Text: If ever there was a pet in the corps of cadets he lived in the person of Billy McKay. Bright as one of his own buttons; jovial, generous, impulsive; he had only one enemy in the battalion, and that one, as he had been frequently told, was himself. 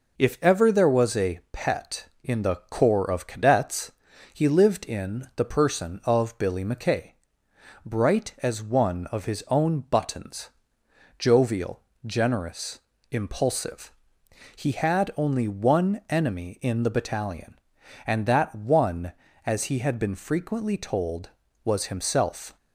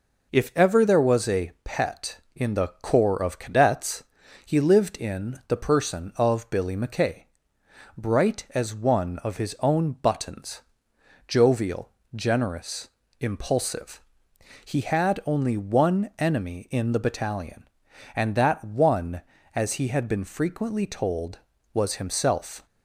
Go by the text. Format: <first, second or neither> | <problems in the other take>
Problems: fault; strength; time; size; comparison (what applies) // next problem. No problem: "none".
neither | pauses between "cadets" and "he"; the same in both